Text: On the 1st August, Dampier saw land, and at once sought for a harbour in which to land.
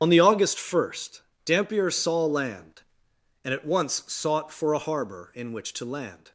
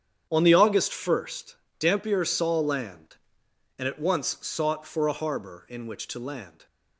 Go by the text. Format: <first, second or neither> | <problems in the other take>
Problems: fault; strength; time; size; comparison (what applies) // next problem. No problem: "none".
second | loses the start of "On"; at 0.0 s; 60 ms // starts louder than the rest; strong; until 1.0 s; 8.5 dB; strong in the second